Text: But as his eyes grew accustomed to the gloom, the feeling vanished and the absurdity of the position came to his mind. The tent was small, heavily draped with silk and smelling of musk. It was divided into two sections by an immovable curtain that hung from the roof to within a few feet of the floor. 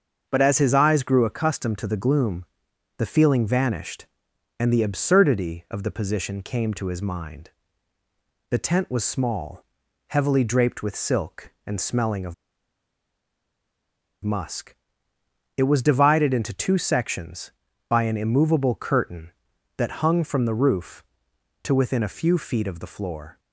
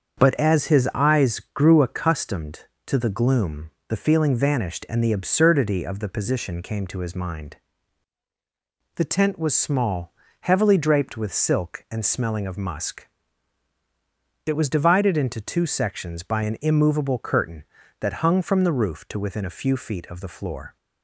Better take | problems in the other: second | starts louder than the rest; until 1.3 s; 7 dB; also in the second // pauses between "of" and "musk"; strong; at 12.3 s; 1.9 s long

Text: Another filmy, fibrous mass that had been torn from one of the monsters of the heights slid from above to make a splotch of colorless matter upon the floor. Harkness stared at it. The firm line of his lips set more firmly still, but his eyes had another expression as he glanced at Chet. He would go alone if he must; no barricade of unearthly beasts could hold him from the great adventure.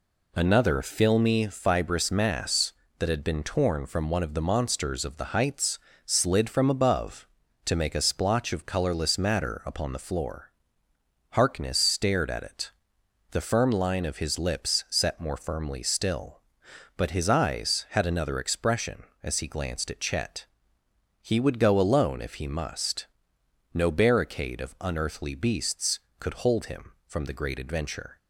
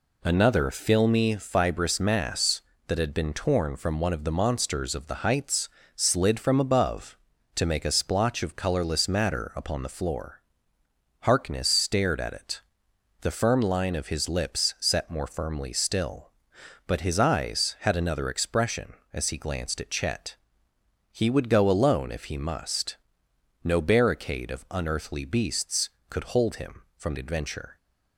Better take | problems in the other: first | pauses between "heights" and "slid"; slight; at 5.6 s; 0.26 s long; slight in the first // skips "the great"; at 27.1 s

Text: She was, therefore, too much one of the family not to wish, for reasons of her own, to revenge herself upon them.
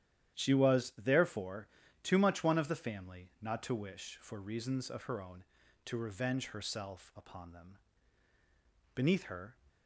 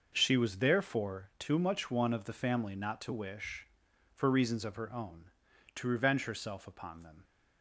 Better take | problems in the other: second | starts louder than the rest; strong; until 1.4 s; 11 dB // goes on to say "Beneath her"; noticeable; from 8.9 s on; 0.62 s long

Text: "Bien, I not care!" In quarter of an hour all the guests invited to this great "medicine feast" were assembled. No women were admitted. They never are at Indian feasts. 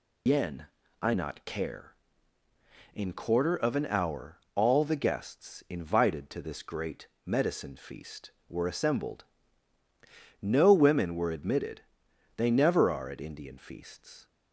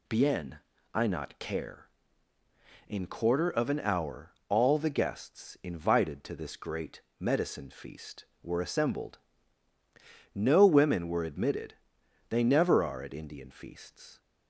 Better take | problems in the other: second | loses the start of "Bien"; at 0.2 s; 110 ms // pauses between "great" and "medicine"; slight; at 7.0 s; 0.16 s long; slight in the second

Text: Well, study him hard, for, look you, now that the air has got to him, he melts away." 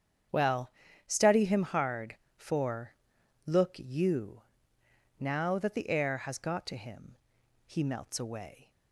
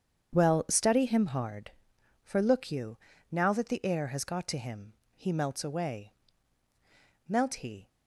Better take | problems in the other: first | starts louder than the rest; strong; until 1.3 s; 8 dB; strong in the first // goes on to say "Melt he"; from 7.2 s on; 0.60 s long

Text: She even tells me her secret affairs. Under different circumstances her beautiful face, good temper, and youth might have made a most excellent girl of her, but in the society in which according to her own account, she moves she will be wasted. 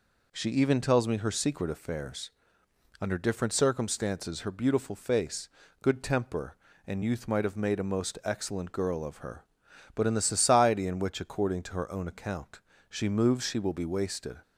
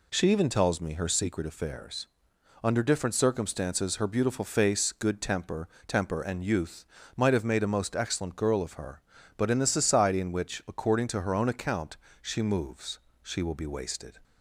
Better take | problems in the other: first | says "temper" twice; at 5.8 s // pauses between "youth" and "might"; slight; at 6.8 s; 0.32 s long // pauses between "moves" and "she"; slight; at 12.9 s; 0.24 s long

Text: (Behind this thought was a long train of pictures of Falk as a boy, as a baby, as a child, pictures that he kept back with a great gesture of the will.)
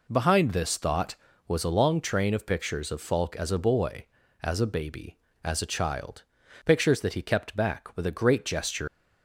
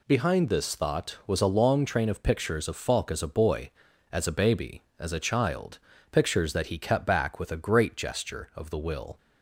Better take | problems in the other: second | stops before "of the will"; at 8.8 s

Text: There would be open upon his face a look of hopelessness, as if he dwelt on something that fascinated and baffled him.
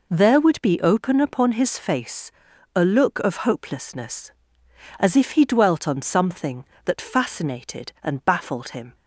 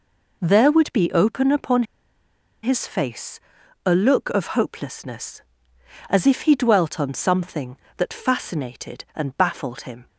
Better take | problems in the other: first | pauses between "upon" and "his"; noticeable; at 1.8 s; 0.79 s long // pauses between "face" and "a"; noticeable; at 3.3 s; 0.46 s long; also in the first

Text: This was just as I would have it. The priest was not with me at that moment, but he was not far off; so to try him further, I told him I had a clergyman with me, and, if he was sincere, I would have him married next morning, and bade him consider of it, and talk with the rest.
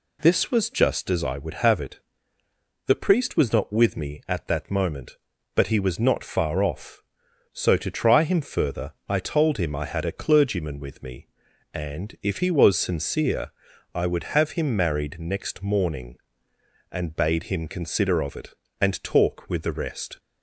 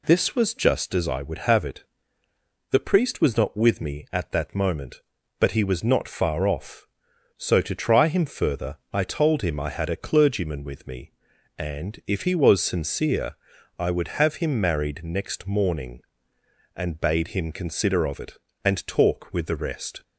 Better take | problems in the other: neither | none

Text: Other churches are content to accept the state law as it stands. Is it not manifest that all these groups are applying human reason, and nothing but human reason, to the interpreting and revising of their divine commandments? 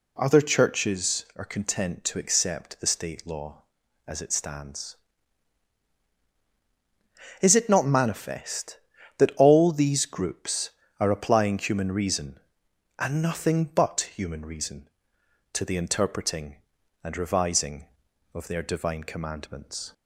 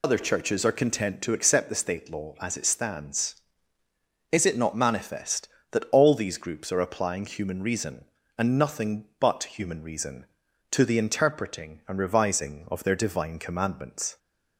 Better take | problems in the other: first | loses the start of "Other"; at 0.0 s; 70 ms

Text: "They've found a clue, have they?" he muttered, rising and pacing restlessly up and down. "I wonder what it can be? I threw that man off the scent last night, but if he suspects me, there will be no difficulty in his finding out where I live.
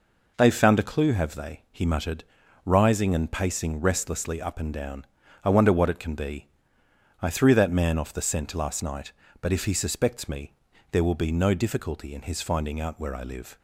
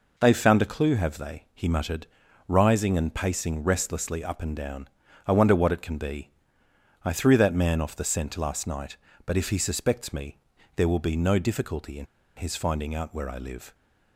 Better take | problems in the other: first | pauses between "in" and "his"; slight; at 12.0 s; 0.30 s long

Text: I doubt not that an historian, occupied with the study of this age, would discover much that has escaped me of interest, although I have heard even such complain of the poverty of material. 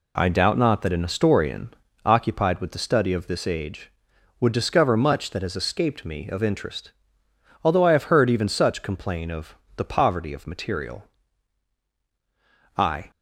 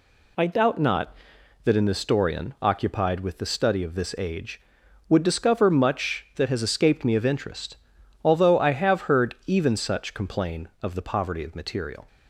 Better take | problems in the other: second | pauses between "of" and "the"; slight; at 9.5 s; 0.20 s long // goes on to say "I"; slight; from 12.7 s on; 0.32 s long

